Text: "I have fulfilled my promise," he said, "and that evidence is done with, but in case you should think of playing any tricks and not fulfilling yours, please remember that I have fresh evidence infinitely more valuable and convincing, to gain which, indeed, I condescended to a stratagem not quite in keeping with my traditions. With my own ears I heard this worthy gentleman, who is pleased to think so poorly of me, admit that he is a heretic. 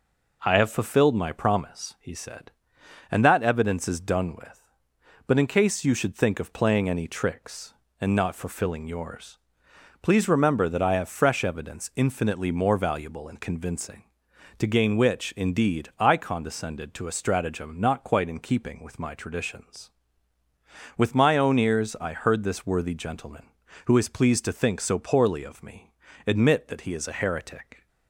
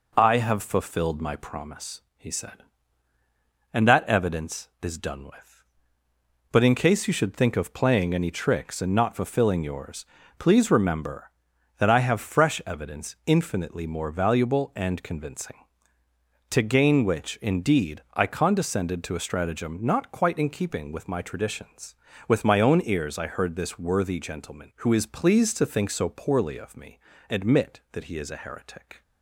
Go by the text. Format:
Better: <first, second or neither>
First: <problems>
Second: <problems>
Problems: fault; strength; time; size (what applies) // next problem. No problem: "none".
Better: neither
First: none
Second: none